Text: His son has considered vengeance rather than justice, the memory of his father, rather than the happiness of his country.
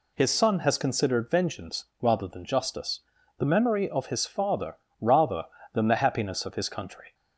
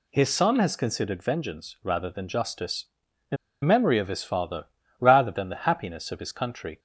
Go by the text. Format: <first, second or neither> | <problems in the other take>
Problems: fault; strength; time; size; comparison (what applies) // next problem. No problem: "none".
first | pauses between "the" and "memory"; slight; at 3.3 s; 0.26 s long